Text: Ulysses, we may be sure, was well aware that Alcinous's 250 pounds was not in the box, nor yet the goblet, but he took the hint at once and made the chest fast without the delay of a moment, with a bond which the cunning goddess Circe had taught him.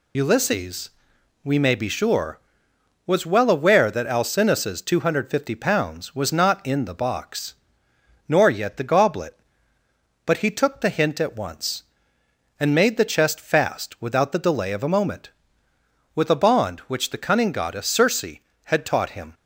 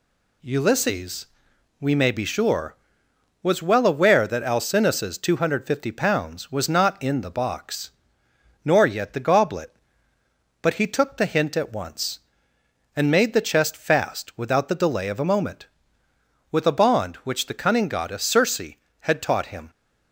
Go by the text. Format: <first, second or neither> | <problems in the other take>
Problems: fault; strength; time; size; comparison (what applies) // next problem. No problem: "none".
second | loses the start of "Ulysses"; at 0.1 s; 95 ms